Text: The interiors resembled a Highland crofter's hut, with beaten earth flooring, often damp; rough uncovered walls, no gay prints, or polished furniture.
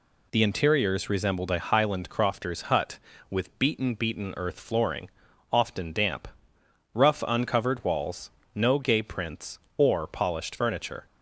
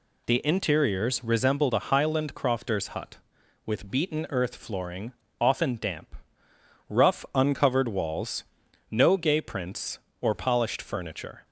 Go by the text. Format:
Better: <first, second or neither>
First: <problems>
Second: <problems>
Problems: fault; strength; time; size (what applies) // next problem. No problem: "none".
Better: second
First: says "beaten" twice; at 3.9 s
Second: none